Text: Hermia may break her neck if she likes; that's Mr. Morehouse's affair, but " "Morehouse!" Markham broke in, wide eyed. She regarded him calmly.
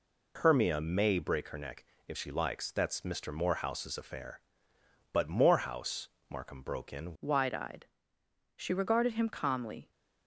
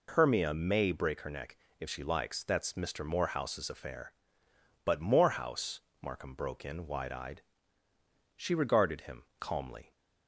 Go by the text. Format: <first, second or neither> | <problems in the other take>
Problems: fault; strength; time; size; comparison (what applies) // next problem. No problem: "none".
second | pauses between "neck" and "if"; slight; at 1.8 s; 0.22 s long; slight in the second // changes voice at "wide"; from 7.2 s on; 2.7 s long